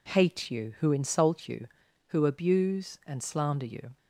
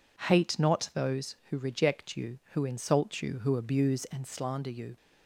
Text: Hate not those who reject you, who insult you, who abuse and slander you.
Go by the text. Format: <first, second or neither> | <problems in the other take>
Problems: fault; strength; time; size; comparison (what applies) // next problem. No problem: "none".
second | skips "not those who reject"; at 0.5 s